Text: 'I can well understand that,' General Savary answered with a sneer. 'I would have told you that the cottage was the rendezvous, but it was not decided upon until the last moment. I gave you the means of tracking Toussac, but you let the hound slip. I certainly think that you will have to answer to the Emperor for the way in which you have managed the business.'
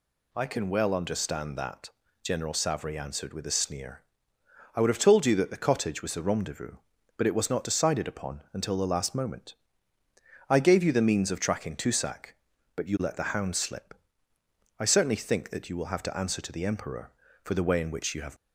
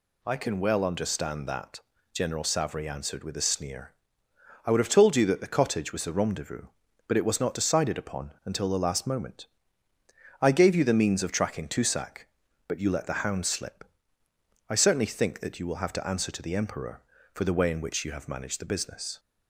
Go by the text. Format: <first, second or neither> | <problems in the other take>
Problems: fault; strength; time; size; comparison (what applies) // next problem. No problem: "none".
second | stops before "managed the business"; at 18.3 s